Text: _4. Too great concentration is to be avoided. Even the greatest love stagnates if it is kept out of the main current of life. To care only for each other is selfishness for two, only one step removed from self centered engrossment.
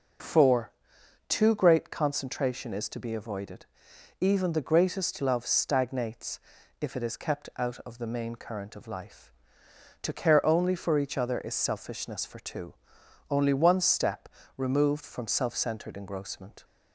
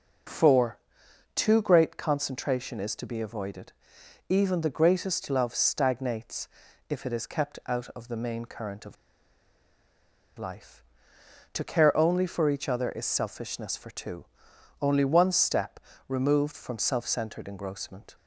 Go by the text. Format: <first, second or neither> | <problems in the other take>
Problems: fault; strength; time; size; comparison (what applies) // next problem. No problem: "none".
first | pauses between "stagnates" and "if"; at 6.4 s; 0.40 s long; also in the first // pauses between "of" and "life"; strong; at 8.9 s; 1.4 s long // pauses between "step" and "removed"; slight; at 15.7 s; 0.28 s long; slight in the first